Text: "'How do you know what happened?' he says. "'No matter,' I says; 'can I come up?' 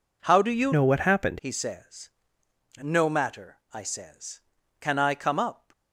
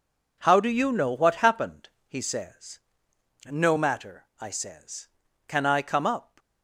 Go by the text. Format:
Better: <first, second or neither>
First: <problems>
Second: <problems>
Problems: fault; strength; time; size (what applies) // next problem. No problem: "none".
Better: second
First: changes voice from "know" to "happened"; from 0.7 to 1.3 s; 0.6 s long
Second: none